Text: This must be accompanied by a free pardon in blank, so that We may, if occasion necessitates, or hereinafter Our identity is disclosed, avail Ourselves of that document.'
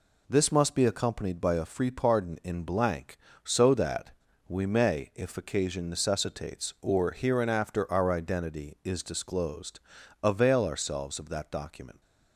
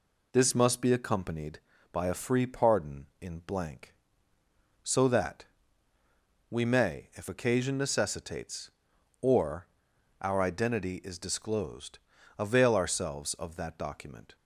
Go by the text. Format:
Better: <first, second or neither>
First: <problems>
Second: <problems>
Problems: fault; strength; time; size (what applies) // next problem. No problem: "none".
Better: first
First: pauses between "that" and "We"; at 4.1 s; 0.39 s long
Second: pauses between "that" and "We"; at 5.4 s; 1.0 s long // skips "hereinafter"; at 9.9 s